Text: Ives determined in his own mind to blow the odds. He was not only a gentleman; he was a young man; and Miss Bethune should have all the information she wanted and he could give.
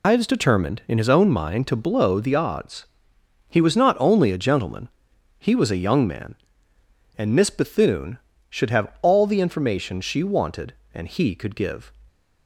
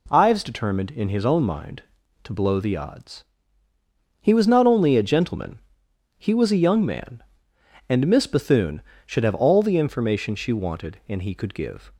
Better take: second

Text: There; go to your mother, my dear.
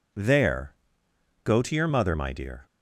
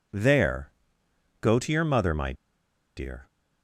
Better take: first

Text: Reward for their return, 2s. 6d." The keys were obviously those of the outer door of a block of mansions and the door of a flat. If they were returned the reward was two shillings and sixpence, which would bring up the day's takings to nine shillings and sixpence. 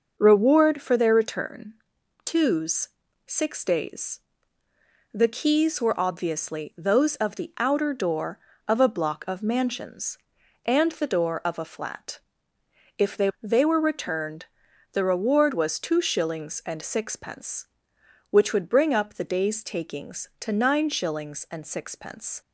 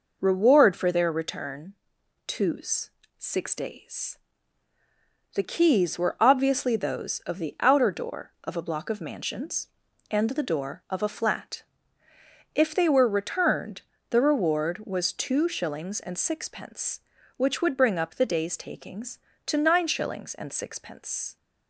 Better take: second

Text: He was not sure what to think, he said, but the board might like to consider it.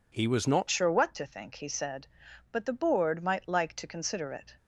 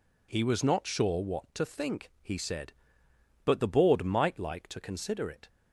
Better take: second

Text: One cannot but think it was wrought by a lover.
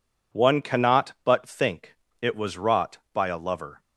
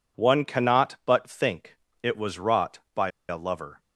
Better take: first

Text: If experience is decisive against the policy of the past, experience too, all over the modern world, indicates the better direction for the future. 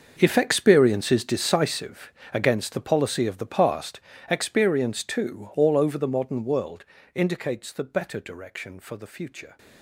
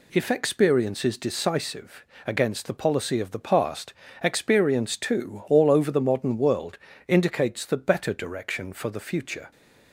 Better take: second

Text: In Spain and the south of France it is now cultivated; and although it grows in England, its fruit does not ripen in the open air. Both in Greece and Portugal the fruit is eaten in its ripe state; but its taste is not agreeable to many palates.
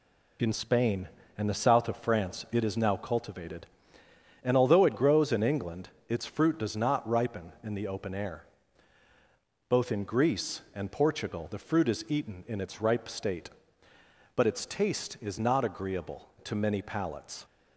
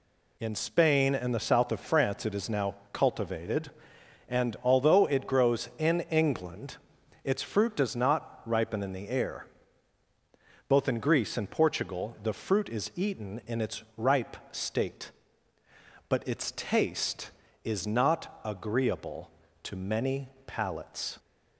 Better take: first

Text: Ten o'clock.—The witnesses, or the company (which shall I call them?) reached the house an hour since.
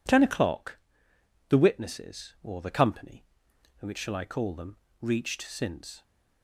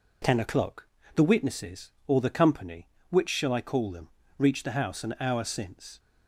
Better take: second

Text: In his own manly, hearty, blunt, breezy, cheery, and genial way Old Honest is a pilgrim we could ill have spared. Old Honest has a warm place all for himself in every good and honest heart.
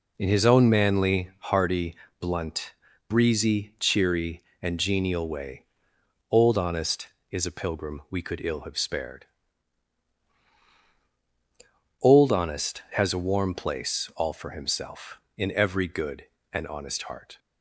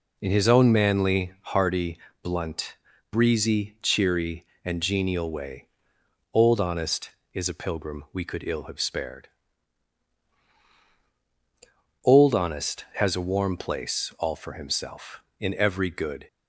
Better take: first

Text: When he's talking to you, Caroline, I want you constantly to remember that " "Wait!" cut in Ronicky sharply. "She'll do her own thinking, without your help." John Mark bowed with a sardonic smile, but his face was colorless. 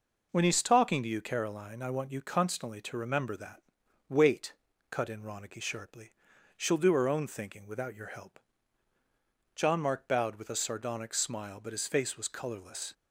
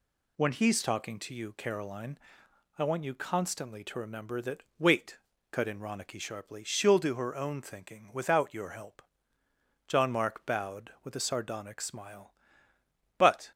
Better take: first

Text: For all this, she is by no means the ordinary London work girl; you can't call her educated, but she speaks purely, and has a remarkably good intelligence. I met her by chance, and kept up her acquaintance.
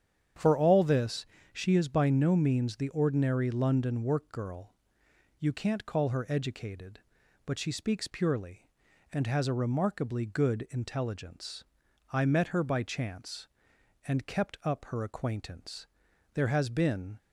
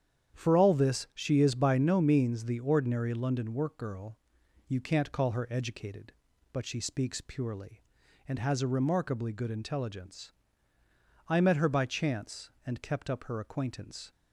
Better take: second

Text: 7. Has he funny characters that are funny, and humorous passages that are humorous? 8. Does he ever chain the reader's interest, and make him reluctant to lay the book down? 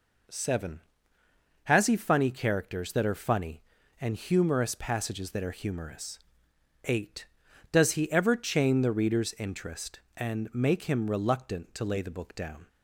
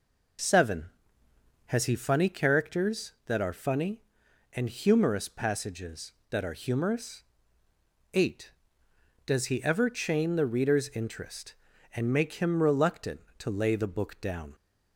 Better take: neither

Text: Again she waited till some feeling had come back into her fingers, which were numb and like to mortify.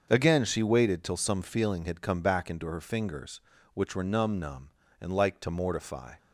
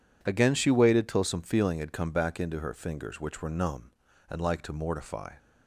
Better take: second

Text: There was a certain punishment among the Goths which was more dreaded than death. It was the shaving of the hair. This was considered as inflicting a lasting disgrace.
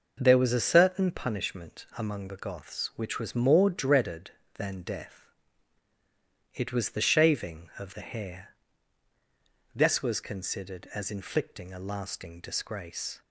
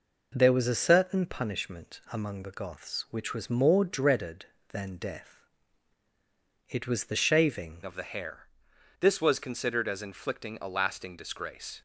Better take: first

